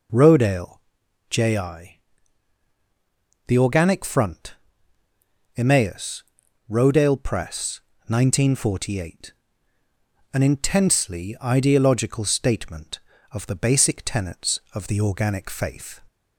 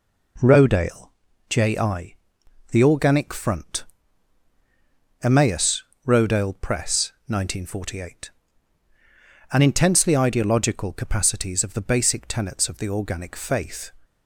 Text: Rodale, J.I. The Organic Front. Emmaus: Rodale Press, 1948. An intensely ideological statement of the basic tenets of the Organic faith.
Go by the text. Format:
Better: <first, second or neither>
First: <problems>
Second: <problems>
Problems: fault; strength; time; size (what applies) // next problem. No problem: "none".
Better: first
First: none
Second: says "capacities" for "statement"; at 10.9 s